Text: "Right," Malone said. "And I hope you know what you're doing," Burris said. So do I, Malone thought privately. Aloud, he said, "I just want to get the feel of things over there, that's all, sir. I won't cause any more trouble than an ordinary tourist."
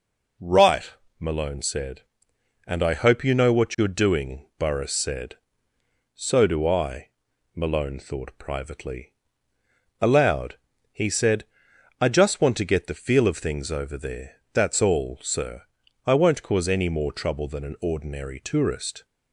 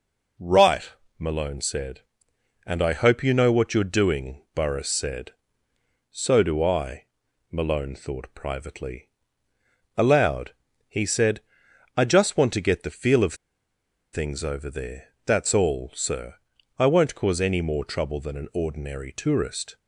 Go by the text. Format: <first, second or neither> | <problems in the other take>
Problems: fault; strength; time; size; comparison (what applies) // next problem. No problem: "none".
first | pauses between "of" and "things"; noticeable; at 13.3 s; 0.77 s long